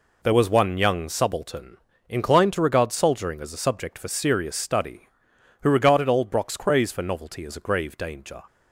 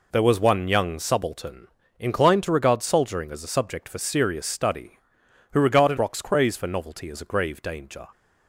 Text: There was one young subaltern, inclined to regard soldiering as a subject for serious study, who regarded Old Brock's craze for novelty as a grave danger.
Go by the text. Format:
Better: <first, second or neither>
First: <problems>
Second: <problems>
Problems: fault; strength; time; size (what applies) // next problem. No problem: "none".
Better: first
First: none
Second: skips "Old"; at 5.9 s